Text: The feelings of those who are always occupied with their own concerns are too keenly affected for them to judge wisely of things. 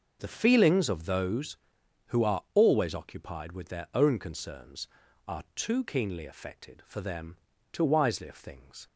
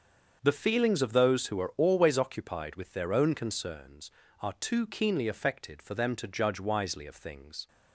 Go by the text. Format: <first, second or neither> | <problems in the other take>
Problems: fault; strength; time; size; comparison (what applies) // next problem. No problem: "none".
second | starts louder than the rest; noticeable; until 1.2 s; 6 dB; also in the second // skips "judge"; at 7.8 s